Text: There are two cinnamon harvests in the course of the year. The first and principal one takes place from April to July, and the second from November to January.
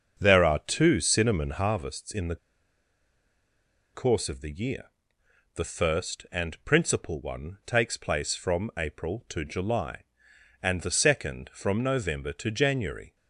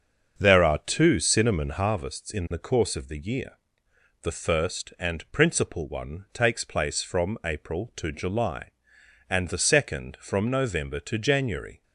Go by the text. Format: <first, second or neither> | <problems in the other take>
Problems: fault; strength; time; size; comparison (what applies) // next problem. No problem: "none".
second | starts louder than the rest; until 1.2 s; 6.5 dB; also in the second // pauses between "the" and "course"; strong; at 2.3 s; 1.5 s long